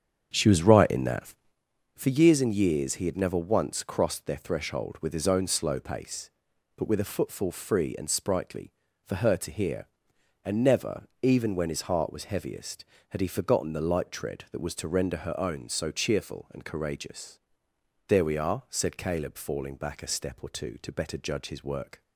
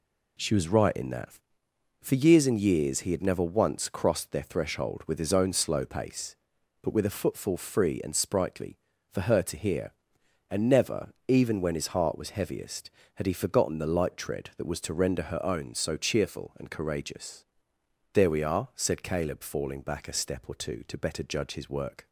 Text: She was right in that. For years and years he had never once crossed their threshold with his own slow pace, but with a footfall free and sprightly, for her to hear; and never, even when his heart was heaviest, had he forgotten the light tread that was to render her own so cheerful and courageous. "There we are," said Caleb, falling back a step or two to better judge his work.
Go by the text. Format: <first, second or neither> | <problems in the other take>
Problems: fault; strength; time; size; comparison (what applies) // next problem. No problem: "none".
second | starts louder than the rest; strong; until 1.6 s; 8 dB